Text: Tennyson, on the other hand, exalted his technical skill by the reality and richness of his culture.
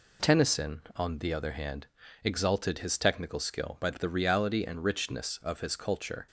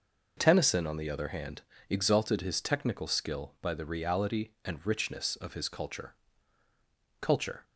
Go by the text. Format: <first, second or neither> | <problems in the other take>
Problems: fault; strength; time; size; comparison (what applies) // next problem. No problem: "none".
first | says "culture" twice; at 7.1 s